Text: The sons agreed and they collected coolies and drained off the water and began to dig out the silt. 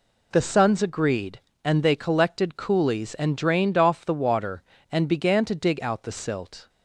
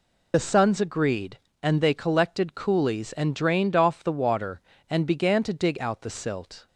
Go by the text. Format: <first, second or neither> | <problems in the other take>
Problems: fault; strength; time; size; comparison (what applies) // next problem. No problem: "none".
first | loses the start of "The"; at 0.3 s; 30 ms